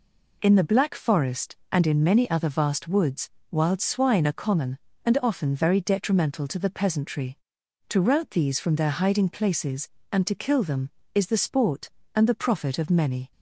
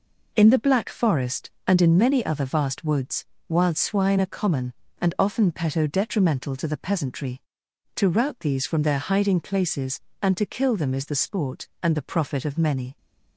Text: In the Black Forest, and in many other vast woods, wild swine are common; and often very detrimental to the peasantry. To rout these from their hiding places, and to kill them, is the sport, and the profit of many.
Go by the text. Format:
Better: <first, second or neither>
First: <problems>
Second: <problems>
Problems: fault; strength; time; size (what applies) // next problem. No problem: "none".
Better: first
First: none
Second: says "peto" for "very"; at 5.5 s